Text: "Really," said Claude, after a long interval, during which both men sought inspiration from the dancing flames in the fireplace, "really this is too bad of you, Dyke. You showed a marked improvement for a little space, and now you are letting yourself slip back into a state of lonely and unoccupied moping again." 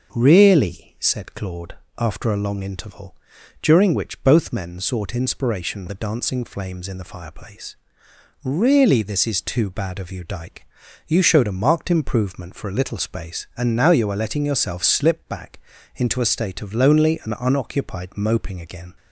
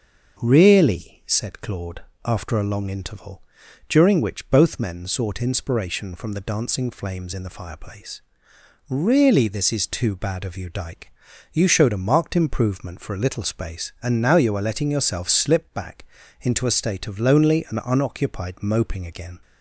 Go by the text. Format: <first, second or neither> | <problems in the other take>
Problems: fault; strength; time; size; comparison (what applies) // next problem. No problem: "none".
second | starts louder than the rest; until 1.1 s; 6.5 dB; also in the second // skips "from"; at 5.8 s // pauses between "back" and "into"; slight; at 15.5 s; 0.36 s long; slight in the second